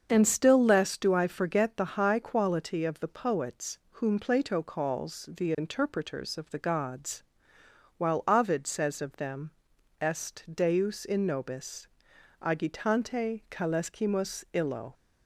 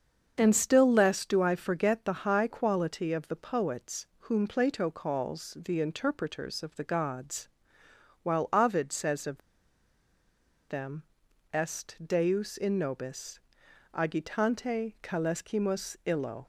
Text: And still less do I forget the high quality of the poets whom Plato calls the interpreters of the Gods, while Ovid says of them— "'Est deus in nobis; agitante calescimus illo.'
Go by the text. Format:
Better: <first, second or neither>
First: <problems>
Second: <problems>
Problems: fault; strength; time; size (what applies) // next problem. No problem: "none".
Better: first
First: starts louder than the rest; until 1.1 s; 7 dB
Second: starts louder than the rest; until 1.3 s; 7 dB // pauses between "of" and "them"; strong; at 9.4 s; 1.2 s long